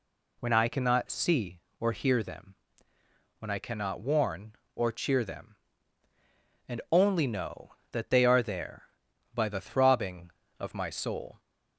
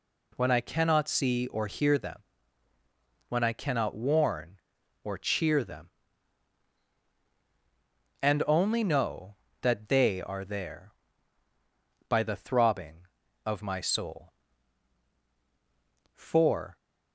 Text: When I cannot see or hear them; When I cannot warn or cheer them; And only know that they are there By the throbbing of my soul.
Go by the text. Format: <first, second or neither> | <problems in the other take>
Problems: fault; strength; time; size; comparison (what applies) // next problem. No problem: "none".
first | goes on to say "For"; noticeable; from 16.1 s on; 0.62 s long